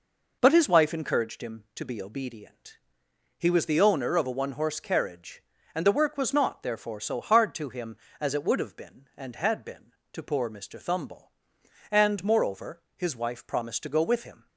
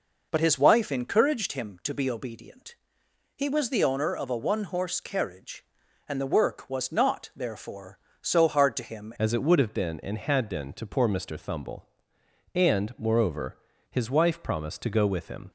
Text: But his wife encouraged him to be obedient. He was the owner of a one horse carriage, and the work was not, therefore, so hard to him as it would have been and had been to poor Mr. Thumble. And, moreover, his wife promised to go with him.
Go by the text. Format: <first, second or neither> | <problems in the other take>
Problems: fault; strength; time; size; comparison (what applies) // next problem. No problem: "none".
first | changes voice at "as"; from 9.1 s on; 6.4 s long